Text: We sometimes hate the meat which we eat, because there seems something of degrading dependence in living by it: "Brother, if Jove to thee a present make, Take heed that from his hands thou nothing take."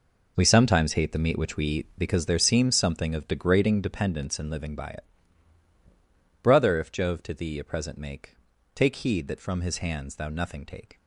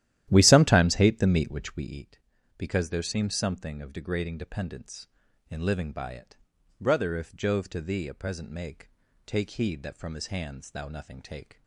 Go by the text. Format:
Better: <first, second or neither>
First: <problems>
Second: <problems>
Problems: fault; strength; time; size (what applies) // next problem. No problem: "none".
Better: first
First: none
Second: starts louder than the rest; strong; until 2.0 s; 12.5 dB